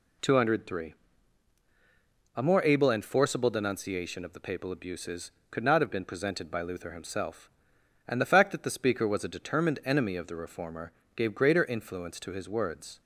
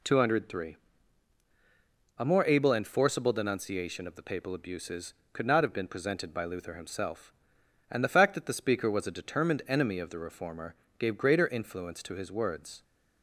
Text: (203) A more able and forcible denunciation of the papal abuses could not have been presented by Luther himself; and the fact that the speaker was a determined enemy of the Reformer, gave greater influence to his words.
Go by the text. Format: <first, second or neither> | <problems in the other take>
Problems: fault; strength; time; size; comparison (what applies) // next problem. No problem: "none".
neither | none